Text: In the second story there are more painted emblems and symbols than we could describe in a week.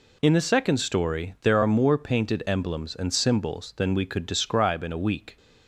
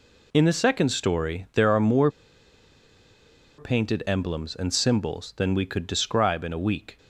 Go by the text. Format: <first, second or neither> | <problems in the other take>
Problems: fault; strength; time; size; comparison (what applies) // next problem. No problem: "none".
first | pauses between "more" and "painted"; strong; at 2.0 s; 1.4 s long